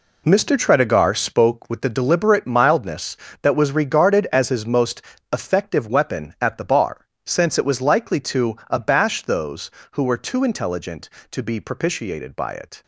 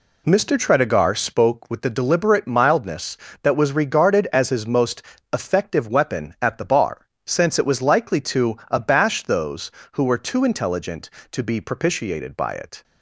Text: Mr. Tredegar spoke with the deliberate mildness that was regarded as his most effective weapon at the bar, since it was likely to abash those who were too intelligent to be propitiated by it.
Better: second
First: gets quieter; strong; throughout; 10.5 dB // pauses between "most" and "effective"; slight; at 5.0 s; 0.28 s long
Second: pauses between "most" and "effective"; slight; at 5.0 s; 0.28 s long

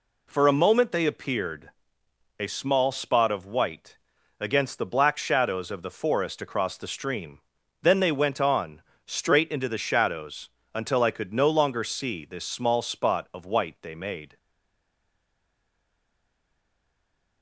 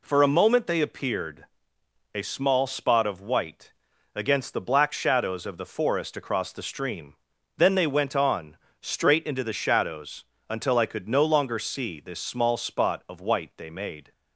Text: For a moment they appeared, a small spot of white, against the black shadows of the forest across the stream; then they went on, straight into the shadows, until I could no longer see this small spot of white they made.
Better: second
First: stays silent after the last word; strong; from 14.3 s on; 3.1 s long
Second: none

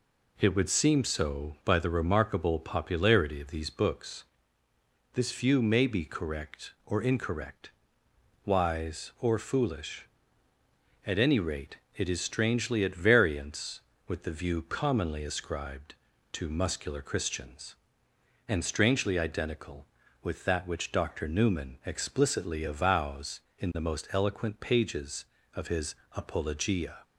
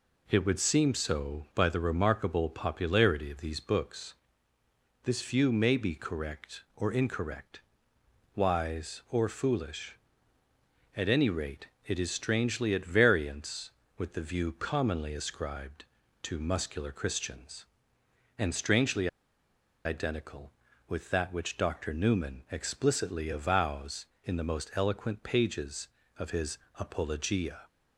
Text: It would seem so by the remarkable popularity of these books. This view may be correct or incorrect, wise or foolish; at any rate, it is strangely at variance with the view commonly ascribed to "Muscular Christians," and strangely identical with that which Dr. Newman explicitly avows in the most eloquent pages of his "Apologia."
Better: first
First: pauses between "his" and "Apologia"; slight; at 25.9 s; 0.18 s long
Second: pauses between "strangely" and "identical"; noticeable; at 19.0 s; 0.78 s long // pauses between "his" and "Apologia"; slight; at 26.5 s; 0.18 s long

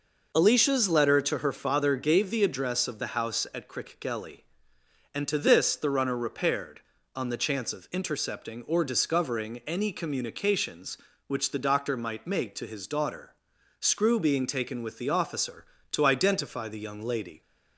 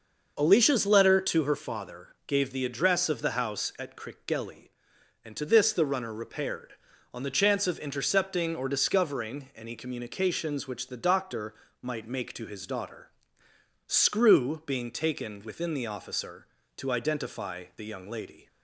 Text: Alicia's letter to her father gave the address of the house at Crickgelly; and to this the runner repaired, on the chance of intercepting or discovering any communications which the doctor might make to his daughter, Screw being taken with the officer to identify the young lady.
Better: first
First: none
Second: pauses between "doctor" and "might"; slight; at 11.5 s; 0.28 s long // says "within" for "with"; at 15.4 s

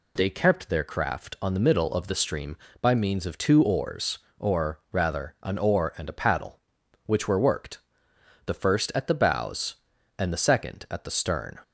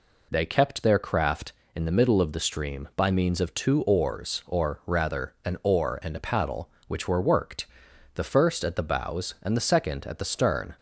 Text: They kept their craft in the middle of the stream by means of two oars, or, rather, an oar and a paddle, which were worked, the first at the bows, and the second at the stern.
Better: second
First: says "on" for "in"; at 1.4 s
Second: none

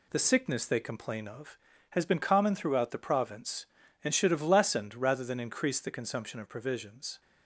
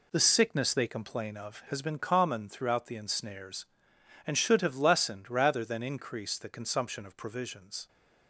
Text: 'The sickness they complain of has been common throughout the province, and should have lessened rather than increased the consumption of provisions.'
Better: first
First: none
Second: says "ensnares" for "province"; at 2.9 s

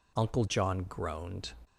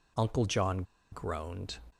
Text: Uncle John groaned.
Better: first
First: none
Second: pauses between "John" and "groaned"; slight; at 0.8 s; 0.28 s long

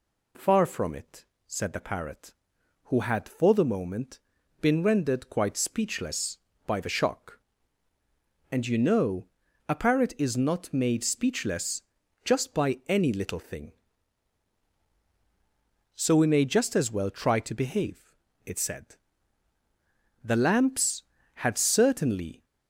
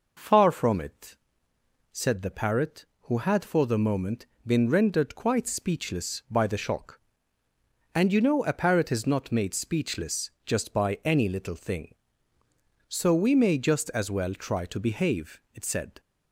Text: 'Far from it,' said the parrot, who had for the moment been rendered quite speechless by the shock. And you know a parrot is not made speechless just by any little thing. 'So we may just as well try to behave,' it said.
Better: second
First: pauses between "moment" and "been"; at 4.1 s; 0.40 s long // pauses between "know" and "a"; at 9.2 s; 0.42 s long // pauses between "speechless" and "just"; at 11.8 s; 0.42 s long // goes on to say "The lamps had certainly"; strong; from 20.2 s on; 2.2 s long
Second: pauses between "moment" and "been"; slight; at 4.2 s; 0.18 s long

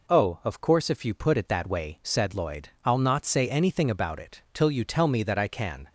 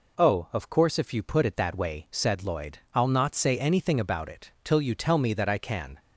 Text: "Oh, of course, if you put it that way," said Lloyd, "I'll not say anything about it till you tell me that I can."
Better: neither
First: none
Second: none

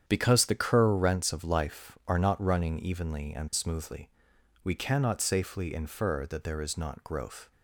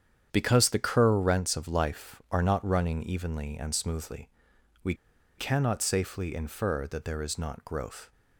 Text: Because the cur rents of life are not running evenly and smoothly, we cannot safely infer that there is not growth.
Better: first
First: starts louder than the rest; strong; until 1.1 s; 9 dB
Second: starts louder than the rest; strong; until 1.3 s; 8.5 dB // pauses between "we" and "cannot"; at 4.9 s; 0.43 s long

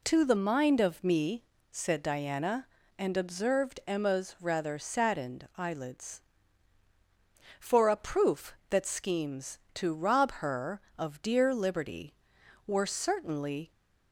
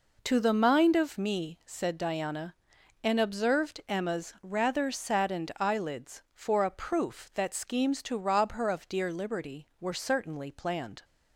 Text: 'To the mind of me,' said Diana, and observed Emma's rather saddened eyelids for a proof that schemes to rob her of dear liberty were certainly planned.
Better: second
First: stops before "planned"; at 13.7 s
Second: none

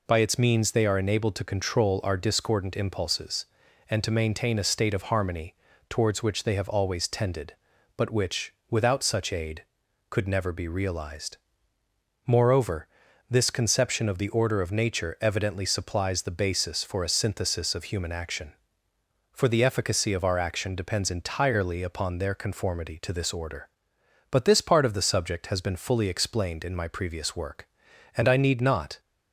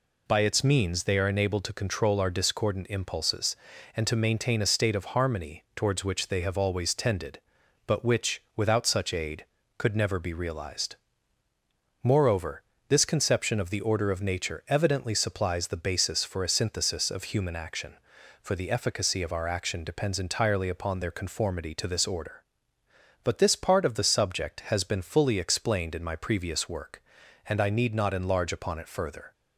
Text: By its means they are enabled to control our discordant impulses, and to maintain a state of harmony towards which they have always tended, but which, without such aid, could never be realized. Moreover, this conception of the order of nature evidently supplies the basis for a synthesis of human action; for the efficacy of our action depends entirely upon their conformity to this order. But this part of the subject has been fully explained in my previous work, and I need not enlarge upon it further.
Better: second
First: pauses between "harmony" and "towards"; slight; at 5.5 s; 0.36 s long // stops before "enlarge upon it further"; at 28.9 s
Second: none

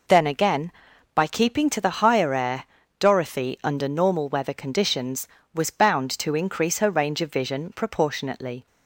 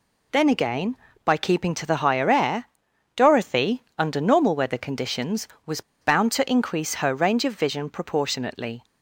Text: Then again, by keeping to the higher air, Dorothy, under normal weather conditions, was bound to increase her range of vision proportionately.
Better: first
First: none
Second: pauses between "was" and "bound"; slight; at 5.7 s; 0.20 s long

